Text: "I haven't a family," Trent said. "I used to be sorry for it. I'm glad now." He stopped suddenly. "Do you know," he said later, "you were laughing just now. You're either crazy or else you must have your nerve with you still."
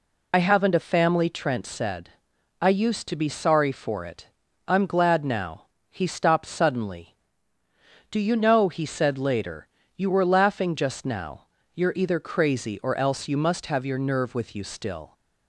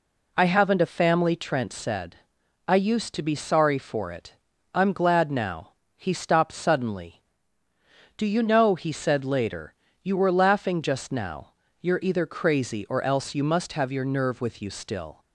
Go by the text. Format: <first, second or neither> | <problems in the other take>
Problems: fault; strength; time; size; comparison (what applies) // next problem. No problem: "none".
second | loses the start of "I"; at 0.3 s; 50 ms